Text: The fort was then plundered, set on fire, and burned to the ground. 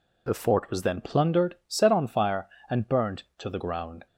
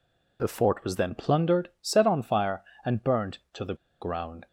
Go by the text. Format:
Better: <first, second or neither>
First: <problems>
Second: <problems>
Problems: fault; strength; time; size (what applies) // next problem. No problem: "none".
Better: first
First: none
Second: pauses between "the" and "ground"; slight; at 3.7 s; 0.26 s long